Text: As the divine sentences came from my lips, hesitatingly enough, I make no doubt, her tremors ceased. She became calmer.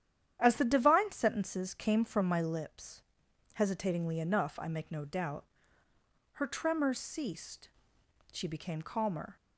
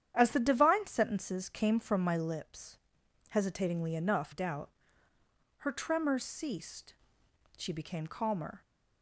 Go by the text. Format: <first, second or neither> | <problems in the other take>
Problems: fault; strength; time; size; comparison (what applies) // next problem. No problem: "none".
first | starts louder than the rest; strong; until 1.1 s; 9.5 dB; strong in the first // skips "I make no"; at 4.3 s